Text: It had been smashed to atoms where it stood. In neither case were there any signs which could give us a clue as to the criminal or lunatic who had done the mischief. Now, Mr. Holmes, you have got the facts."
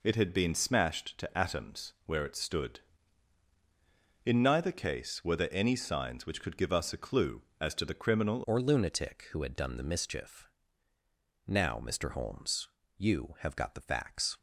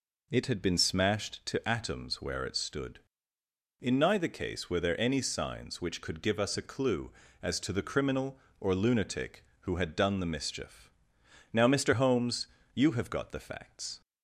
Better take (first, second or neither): second